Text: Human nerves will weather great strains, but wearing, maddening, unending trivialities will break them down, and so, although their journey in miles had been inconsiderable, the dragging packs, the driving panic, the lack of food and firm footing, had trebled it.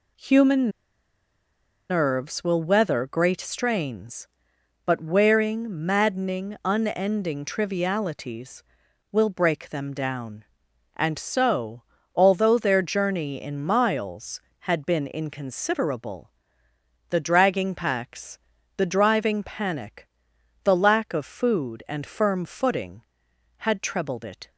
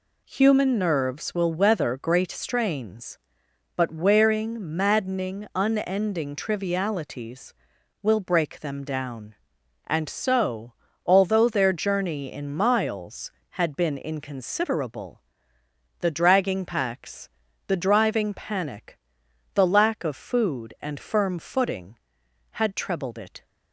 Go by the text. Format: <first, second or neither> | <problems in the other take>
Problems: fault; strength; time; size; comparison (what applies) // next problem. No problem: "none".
second | pauses between "Human" and "nerves"; at 0.7 s; 1.1 s long